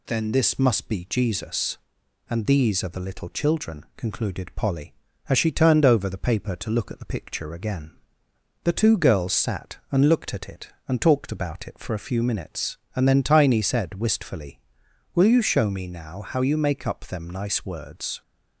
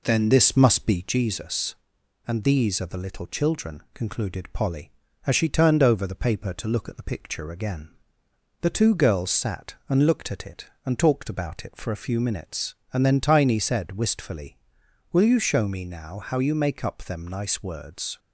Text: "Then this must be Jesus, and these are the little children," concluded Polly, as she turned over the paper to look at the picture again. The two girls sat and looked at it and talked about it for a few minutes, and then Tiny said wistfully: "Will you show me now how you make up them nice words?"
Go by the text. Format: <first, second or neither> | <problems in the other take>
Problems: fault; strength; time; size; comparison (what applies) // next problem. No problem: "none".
first | starts louder than the rest; noticeable; until 1.2 s; 4 dB